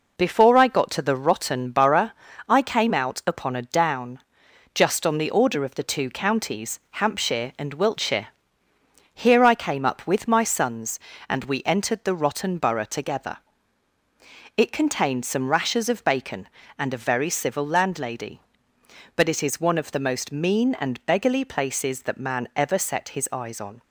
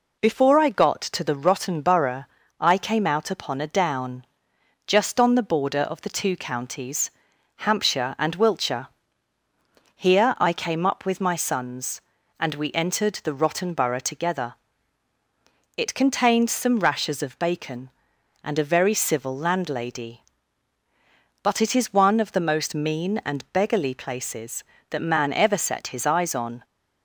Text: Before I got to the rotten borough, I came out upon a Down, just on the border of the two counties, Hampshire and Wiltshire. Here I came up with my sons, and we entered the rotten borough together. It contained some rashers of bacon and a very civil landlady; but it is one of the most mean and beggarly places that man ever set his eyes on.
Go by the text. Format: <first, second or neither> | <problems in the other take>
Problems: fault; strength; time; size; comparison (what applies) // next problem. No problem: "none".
second | says "order" for "border"; at 5.2 s